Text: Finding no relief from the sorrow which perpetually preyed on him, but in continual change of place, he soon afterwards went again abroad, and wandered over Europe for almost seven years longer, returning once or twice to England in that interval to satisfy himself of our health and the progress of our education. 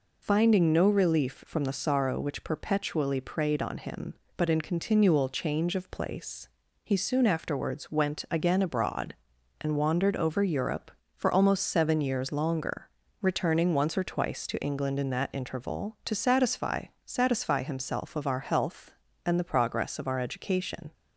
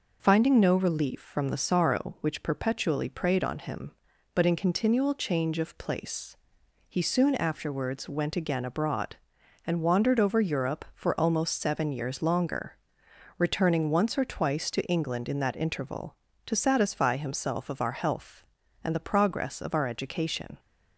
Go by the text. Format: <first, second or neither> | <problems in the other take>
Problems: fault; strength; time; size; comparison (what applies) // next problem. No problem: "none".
second | says "satisfy" twice; at 17.0 s